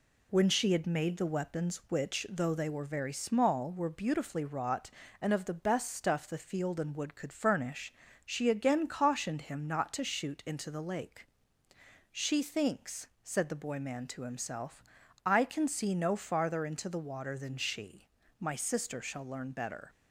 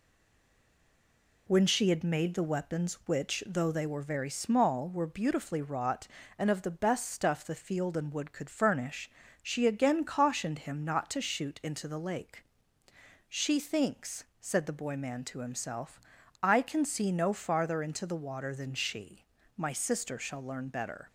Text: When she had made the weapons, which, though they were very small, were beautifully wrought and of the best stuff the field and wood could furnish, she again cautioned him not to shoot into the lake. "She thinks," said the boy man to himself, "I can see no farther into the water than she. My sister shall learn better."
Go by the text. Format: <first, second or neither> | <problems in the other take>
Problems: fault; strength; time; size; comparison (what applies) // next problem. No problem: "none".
first | stays silent before the first word; noticeable; until 1.4 s; 1.4 s long